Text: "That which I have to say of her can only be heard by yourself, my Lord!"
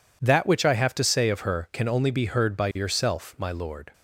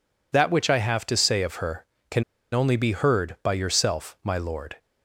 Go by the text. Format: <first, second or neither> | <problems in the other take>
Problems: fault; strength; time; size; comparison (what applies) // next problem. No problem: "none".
first | pauses between "can" and "only"; slight; at 2.2 s; 0.29 s long